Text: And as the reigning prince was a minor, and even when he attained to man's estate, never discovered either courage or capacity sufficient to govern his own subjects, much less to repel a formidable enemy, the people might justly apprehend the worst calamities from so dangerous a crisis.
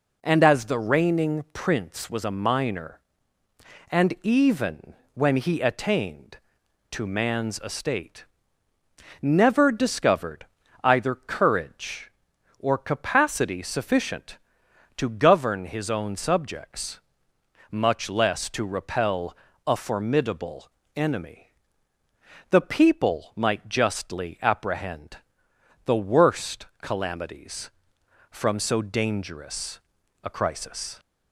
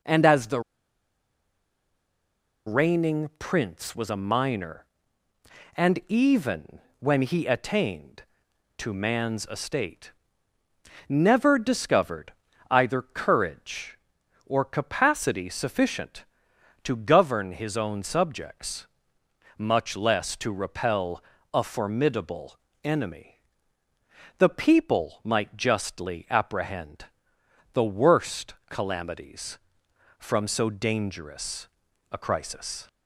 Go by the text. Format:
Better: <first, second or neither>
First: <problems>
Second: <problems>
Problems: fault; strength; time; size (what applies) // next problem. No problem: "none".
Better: first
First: pauses between "even" and "when"; slight; at 4.9 s; 0.20 s long // pauses between "discovered" and "either"; at 10.4 s; 0.38 s long // pauses between "repel" and "a"; slight; at 19.3 s; 0.28 s long // pauses between "formidable" and "enemy"; slight; at 20.6 s; 0.28 s long // pauses between "apprehend" and "the"; noticeable; at 25.1 s; 0.68 s long // pauses between "worst" and "calamities"; slight; at 26.6 s; 0.16 s long // pauses between "dangerous" and "a"; at 29.7 s; 0.44 s long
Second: pauses between "the" and "reigning"; strong; at 0.5 s; 2.0 s long // pauses between "even" and "when"; slight; at 6.7 s; 0.20 s long // pauses between "discovered" and "either"; at 12.3 s; 0.38 s long // pauses between "repel" and "a"; slight; at 21.2 s; 0.28 s long // pauses between "formidable" and "enemy"; slight; at 22.5 s; 0.28 s long // pauses between "apprehend" and "the"; noticeable; at 27.0 s; 0.68 s long // pauses between "worst" and "calamities"; slight; at 28.5 s; 0.16 s long // pauses between "dangerous" and "a"; at 31.6 s; 0.44 s long